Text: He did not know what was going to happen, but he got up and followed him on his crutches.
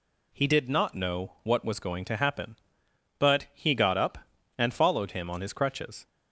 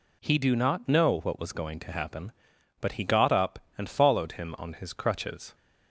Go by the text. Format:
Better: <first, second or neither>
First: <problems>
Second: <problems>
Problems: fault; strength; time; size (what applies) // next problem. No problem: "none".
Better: first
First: none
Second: says "do" for "did"; at 0.3 s